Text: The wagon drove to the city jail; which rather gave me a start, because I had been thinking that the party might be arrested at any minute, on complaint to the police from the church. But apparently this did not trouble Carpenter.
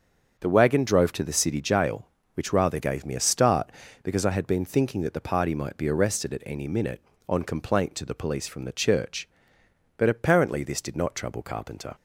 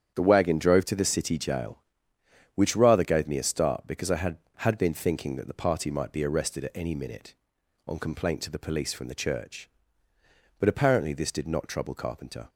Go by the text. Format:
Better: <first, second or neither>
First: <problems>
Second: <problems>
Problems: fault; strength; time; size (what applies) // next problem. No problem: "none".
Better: first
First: starts louder than the rest; until 1.4 s; 7 dB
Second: starts louder than the rest; strong; until 1.1 s; 8.5 dB // says "had" twice; at 4.5 s